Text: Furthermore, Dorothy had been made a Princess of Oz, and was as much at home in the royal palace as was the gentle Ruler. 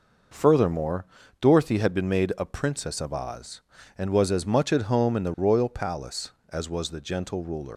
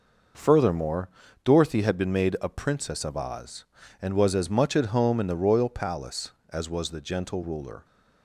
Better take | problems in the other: second | leaves "Ruler" unfinished; at 7.7 s; 105 ms

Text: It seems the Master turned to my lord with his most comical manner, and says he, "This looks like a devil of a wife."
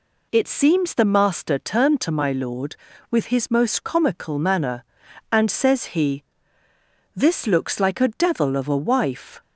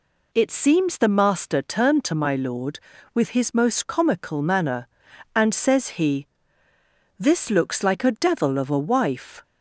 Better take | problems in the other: neither | none

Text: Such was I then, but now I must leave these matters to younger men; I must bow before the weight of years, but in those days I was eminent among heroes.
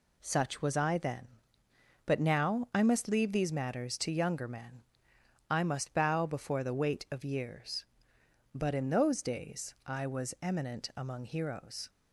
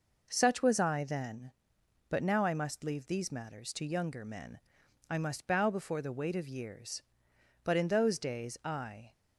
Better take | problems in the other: first | stops before "was eminent among heroes"; at 9.1 s

